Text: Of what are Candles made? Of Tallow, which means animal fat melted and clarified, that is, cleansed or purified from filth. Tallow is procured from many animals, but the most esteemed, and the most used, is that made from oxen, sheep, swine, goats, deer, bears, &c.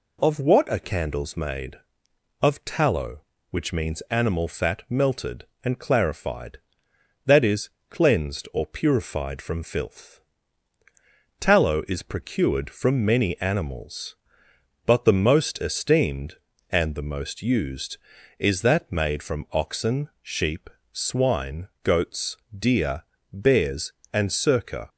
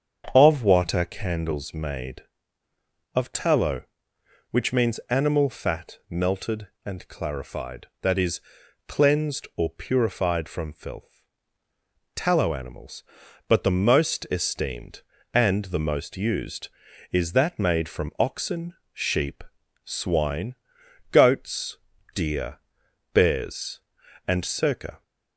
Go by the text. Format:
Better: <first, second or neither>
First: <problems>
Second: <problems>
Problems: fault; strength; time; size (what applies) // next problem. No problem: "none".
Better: first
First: none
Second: starts louder than the rest; strong; until 1.3 s; 7.5 dB // skips "is procured from many"; at 12.5 s